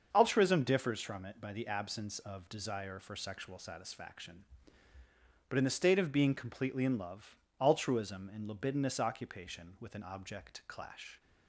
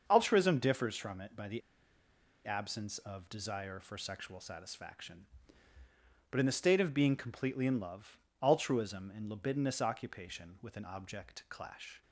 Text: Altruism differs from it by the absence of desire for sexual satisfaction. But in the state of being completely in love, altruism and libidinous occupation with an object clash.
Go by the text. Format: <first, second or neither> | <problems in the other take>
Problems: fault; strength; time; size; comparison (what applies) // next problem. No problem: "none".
first | starts louder than the rest; until 1.0 s; 6.5 dB; also in the first // pauses between "the" and "absence"; noticeable; at 1.6 s; 0.86 s long